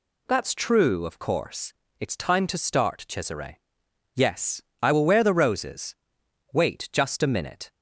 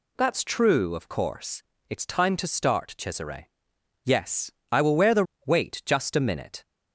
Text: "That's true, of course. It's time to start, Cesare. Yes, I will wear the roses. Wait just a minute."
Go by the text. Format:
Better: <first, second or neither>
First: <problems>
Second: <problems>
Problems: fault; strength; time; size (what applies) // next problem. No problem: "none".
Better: first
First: none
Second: skips "roses"; at 5.3 s